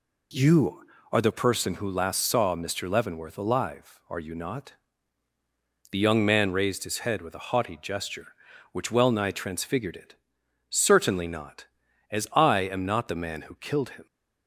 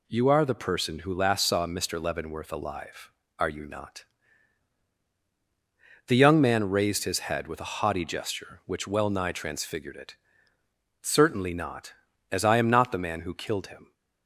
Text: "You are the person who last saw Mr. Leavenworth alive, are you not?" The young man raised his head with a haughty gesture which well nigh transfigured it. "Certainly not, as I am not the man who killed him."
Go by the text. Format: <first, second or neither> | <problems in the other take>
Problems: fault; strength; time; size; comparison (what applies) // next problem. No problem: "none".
neither | none